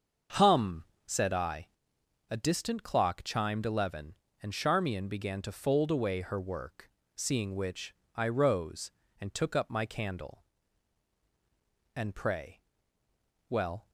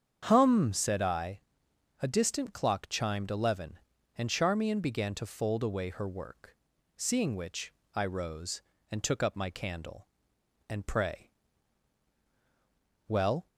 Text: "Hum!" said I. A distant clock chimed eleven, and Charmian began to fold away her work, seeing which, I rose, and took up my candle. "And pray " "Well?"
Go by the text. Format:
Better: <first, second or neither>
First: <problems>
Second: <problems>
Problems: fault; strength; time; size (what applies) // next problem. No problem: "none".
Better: neither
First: starts louder than the rest; until 1.5 s; 6.5 dB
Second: starts louder than the rest; strong; until 1.2 s; 8 dB